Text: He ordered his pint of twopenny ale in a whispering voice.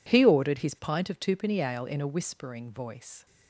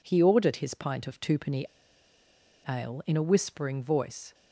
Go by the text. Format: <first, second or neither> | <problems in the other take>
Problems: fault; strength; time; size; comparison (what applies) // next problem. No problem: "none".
first | pauses between "twopenny" and "ale"; at 1.6 s; 1.0 s long